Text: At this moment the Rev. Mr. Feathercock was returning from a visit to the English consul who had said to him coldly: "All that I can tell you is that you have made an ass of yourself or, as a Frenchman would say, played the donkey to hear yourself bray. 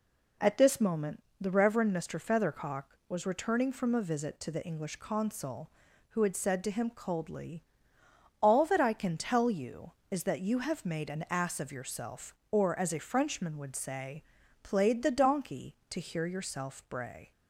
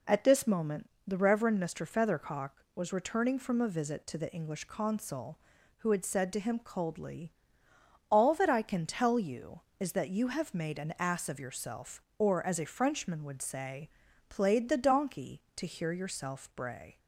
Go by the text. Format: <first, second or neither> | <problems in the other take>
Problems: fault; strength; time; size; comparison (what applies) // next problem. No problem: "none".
neither | pauses between "moment" and "the"; slight; the same in both